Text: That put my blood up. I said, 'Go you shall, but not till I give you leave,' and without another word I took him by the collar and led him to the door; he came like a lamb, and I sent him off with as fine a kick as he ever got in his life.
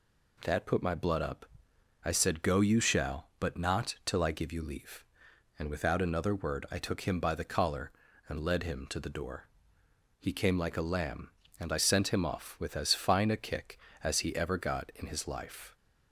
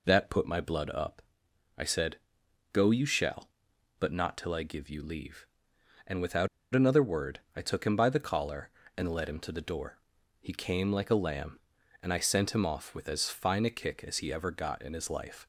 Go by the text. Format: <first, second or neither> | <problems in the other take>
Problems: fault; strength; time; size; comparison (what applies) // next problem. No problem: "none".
first | pauses between "without" and "another"; slight; at 6.4 s; 0.26 s long